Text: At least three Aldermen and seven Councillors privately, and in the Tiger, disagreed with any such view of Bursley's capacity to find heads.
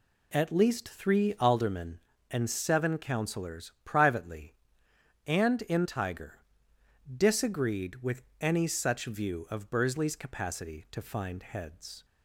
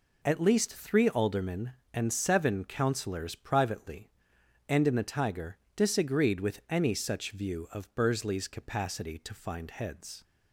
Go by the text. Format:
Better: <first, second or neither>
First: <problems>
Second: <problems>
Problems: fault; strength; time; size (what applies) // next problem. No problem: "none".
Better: second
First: skips "the"; at 5.8 s // pauses between "with" and "any"; slight; at 8.2 s; 0.16 s long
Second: none